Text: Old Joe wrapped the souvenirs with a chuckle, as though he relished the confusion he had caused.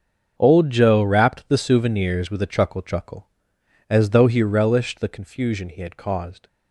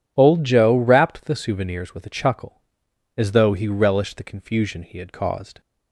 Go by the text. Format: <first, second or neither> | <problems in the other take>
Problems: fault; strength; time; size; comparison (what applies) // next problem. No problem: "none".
second | starts louder than the rest; until 1.3 s; 7 dB // says "chuckle" twice; at 2.8 s